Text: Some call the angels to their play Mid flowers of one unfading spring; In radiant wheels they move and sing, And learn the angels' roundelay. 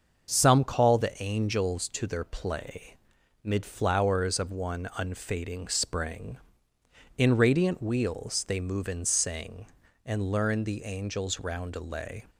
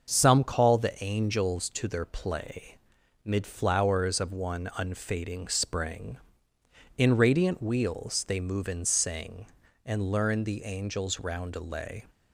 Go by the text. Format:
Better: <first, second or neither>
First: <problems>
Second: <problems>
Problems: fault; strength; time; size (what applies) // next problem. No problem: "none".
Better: neither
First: starts louder than the rest; until 1.3 s; 6.5 dB // pauses between "play" and "Mid"; noticeable; at 2.9 s; 0.46 s long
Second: starts louder than the rest; until 1.1 s; 6.5 dB // pauses between "play" and "Mid"; noticeable; at 2.7 s; 0.46 s long